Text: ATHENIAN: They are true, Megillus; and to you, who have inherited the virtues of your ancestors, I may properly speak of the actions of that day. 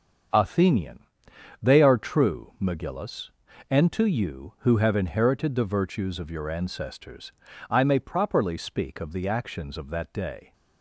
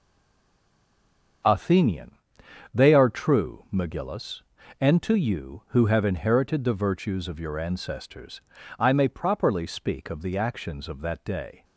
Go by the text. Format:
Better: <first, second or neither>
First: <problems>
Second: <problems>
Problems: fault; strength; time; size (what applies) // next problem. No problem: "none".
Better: first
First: starts louder than the rest; strong; until 1.9 s; 7.5 dB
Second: stays silent before the first word; noticeable; until 1.4 s; 1.4 s long // starts louder than the rest; strong; until 3.0 s; 7.5 dB